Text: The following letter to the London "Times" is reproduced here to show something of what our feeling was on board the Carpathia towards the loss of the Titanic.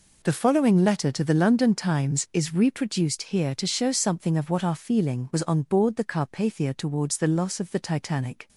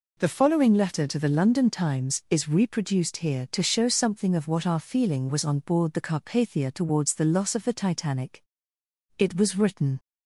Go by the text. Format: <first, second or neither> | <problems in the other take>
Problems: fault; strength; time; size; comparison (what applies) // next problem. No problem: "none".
first | goes on to say "It was written"; noticeable; from 9.1 s on; 0.80 s long